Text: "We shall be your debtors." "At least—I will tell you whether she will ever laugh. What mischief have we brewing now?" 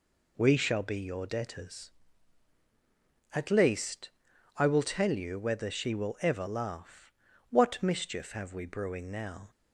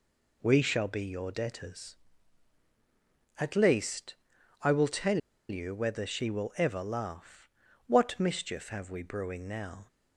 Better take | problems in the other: first | pauses between "tell" and "you"; slight; at 5.1 s; 0.31 s long

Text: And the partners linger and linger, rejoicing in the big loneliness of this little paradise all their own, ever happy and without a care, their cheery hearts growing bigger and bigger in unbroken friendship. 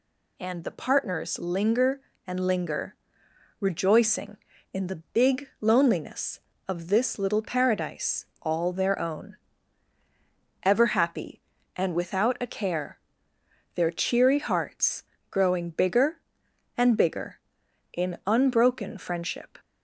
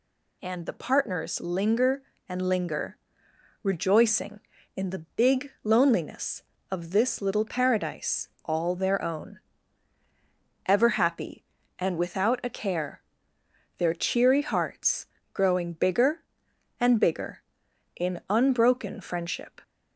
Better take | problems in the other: neither | pauses between "paradise" and "all"; slight; the same in both // pauses between "hearts" and "growing"; slight; the same in both

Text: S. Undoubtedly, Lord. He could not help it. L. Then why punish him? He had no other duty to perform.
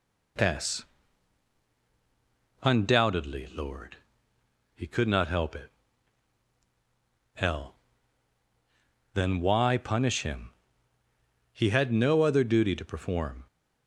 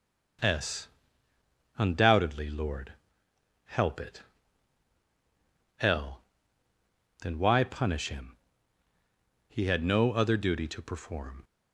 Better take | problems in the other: first | starts louder than the rest; until 2.3 s; 7 dB // skips "He could not"; at 3.2 s

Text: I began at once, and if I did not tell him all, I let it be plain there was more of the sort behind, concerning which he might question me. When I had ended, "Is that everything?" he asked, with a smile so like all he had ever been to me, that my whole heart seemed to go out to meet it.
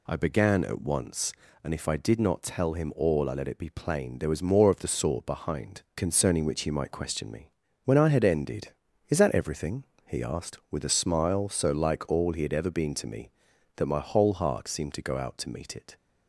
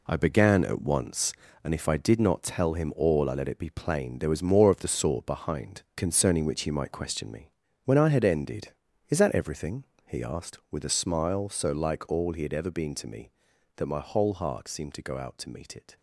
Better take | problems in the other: first | gets quieter; strong; throughout; 8.5 dB

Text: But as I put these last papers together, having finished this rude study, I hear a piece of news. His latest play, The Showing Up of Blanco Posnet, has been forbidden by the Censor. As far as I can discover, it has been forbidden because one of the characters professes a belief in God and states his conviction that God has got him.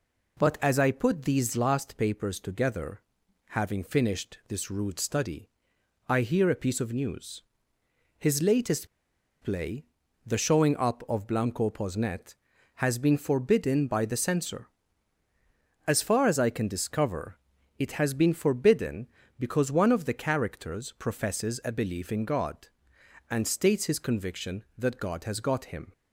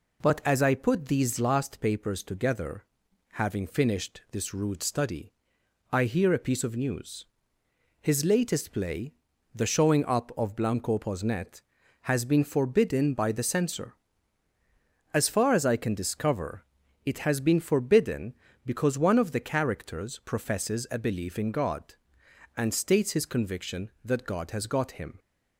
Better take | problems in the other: second | pauses between "latest" and "play"; noticeable; at 8.8 s; 0.54 s long

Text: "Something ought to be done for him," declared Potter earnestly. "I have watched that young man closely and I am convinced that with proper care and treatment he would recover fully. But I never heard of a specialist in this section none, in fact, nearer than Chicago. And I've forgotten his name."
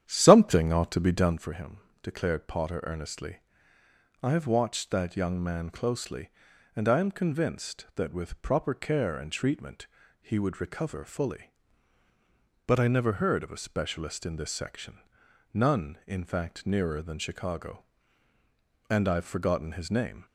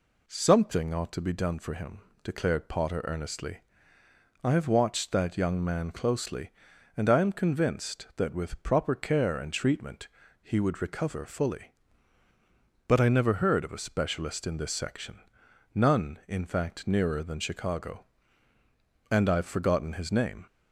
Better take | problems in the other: second | starts louder than the rest; strong; until 1.5 s; 10 dB // pauses between "treatment" and "he"; slight; at 9.8 s; 0.36 s long; slight in the second // pauses between "section" and "none"; noticeable; at 14.9 s; 0.56 s long; noticeable in the second

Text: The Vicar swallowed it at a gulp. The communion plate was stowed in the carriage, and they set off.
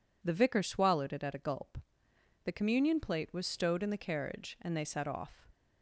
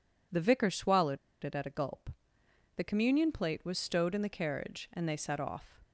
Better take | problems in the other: first | pauses between "swallowed" and "it"; slight; at 1.1 s; 0.26 s long

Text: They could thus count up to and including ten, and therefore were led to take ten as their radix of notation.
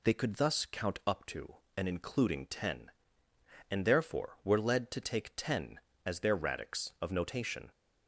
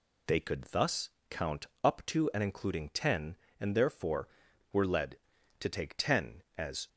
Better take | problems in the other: first | pauses between "thus" and "count"; slight; at 1.0 s; 0.20 s long // pauses between "count" and "up"; slight; at 1.6 s; 0.16 s long // stops before "their radix of notation"; at 6.8 s

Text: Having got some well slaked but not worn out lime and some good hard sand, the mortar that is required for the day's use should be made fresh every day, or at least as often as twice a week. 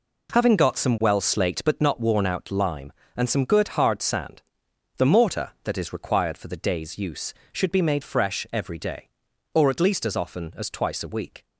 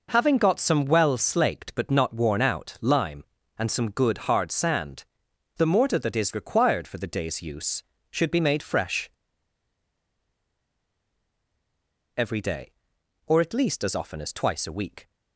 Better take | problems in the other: first | pauses between "fresh" and "every"; strong; at 9.1 s; 3.0 s long

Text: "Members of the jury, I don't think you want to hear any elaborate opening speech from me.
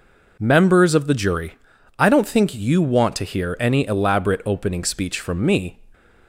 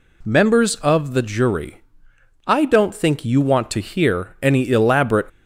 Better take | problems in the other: first | stops before "opening speech from me"; at 5.2 s

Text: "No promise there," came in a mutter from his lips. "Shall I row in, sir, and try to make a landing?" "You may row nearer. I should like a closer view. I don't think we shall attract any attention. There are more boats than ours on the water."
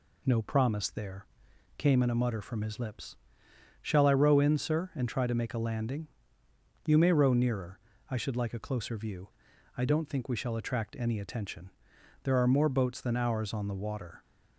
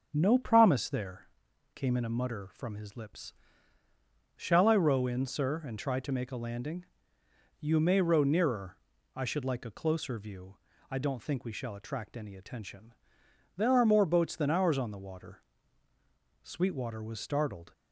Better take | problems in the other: first | starts louder than the rest; until 1.1 s; 6.5 dB // goes on to say "Sweetwater was startled"; noticeable; from 16.4 s on; 1.3 s long

